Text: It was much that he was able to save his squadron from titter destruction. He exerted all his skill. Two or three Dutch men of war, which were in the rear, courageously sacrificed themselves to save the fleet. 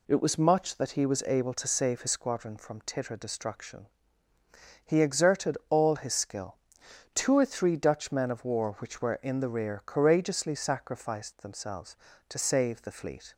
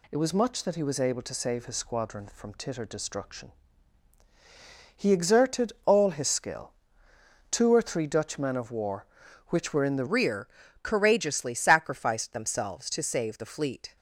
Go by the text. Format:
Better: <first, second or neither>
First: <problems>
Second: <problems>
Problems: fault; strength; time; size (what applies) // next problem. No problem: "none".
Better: first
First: none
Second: changes voice at "rear"; from 10.0 s on; 3.9 s long